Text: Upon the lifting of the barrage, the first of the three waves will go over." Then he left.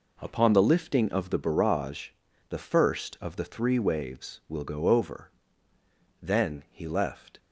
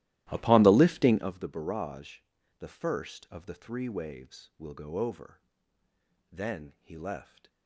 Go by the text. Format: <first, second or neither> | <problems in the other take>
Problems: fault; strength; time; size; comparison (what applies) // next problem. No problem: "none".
first | starts louder than the rest; strong; until 1.3 s; 15 dB